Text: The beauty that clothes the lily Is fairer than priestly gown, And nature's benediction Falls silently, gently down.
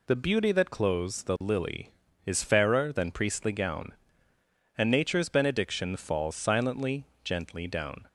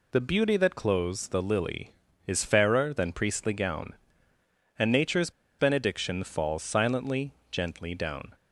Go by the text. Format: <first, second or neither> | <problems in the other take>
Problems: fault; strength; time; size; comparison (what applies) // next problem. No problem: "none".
first | pauses between "nature's" and "benediction"; slight; at 5.3 s; 0.28 s long